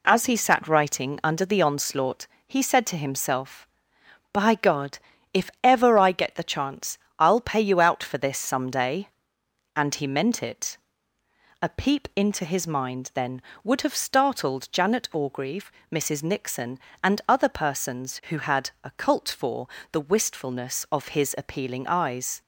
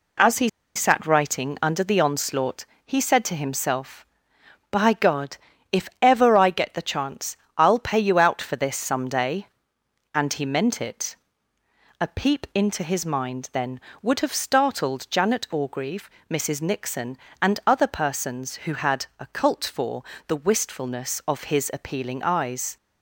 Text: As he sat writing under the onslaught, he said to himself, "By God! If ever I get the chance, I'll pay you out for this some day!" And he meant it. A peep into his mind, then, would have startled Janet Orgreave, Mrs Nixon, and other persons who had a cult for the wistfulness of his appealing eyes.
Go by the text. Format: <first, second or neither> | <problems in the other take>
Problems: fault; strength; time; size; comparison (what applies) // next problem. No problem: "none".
first | pauses between "he" and "sat"; slight; at 0.4 s; 0.27 s long // pauses between "for" and "the"; slight; at 20.0 s; 0.24 s long; slight in the first